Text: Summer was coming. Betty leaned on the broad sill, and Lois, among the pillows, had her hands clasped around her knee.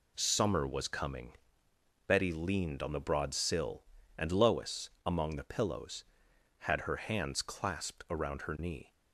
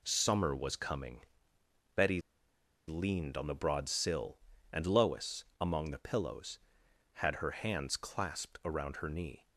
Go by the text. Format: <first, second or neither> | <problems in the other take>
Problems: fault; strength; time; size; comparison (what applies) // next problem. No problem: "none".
first | pauses between "Betty" and "leaned"; noticeable; at 2.1 s; 0.68 s long